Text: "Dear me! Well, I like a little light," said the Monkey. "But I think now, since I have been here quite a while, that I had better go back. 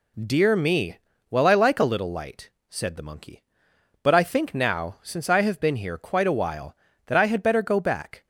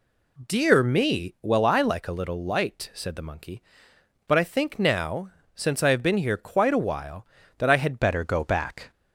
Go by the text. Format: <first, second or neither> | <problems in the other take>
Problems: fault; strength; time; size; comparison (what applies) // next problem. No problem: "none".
first | changes voice at "better"; from 8.0 s on; 0.8 s long